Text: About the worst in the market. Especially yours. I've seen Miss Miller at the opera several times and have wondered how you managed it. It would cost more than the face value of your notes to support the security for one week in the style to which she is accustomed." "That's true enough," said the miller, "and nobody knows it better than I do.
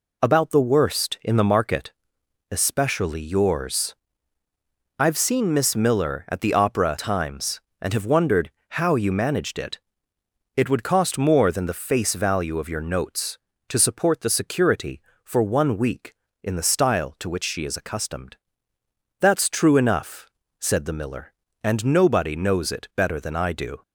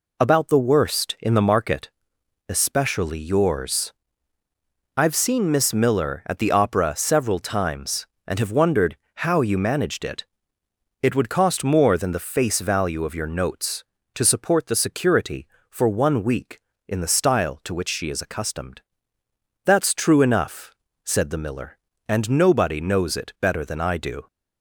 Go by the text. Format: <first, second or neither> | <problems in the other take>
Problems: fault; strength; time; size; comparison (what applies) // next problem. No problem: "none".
second | skips "several"; at 6.9 s // pauses between "wondered" and "how"; slight; at 8.4 s; 0.20 s long; slight in the second